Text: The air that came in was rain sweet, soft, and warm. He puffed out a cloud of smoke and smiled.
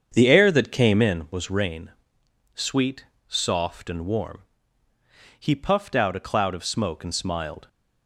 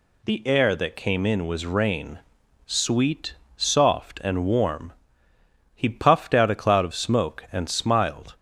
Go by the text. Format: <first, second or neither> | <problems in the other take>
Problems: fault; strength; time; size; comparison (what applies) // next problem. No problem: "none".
second | starts louder than the rest; strong; until 1.3 s; 7.5 dB // pauses between "rain" and "sweet"; noticeable; at 1.9 s; 0.62 s long; noticeable in the second